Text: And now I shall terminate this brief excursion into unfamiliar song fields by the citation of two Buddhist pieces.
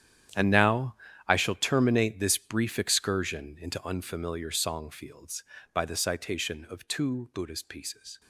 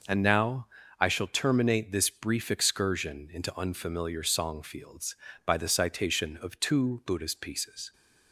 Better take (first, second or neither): second